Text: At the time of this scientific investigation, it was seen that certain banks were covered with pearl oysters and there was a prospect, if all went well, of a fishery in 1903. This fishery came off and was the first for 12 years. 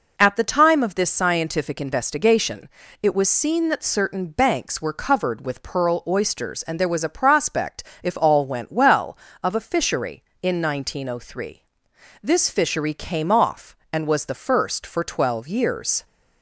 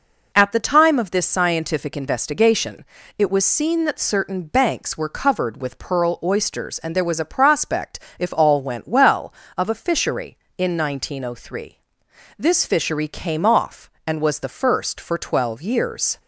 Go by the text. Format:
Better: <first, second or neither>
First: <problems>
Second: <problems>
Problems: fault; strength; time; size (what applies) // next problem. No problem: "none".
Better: neither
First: none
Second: none